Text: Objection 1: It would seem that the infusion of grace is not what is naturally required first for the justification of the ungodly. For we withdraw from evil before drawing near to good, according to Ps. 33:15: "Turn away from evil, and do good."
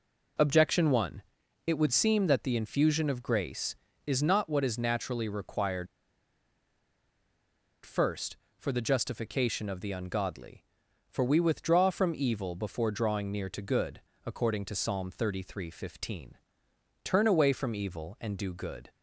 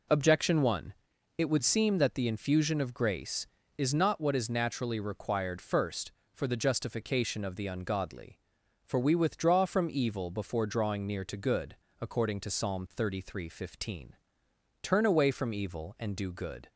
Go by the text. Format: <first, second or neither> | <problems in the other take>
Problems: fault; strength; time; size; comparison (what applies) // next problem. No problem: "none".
second | pauses between "required" and "first"; strong; at 5.8 s; 1.9 s long